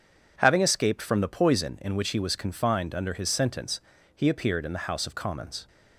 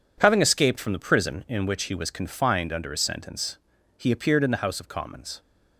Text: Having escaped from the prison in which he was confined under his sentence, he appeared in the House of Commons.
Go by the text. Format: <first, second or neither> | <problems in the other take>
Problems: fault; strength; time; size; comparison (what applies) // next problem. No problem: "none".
second | says "poison" for "prison"; at 1.2 s